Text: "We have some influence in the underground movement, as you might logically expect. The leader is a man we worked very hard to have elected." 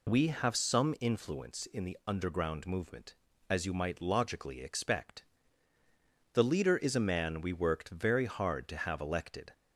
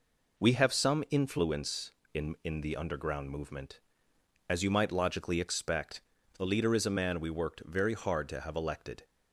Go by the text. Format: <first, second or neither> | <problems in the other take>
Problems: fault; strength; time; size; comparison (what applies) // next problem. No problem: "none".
first | says "in" twice; at 2.4 s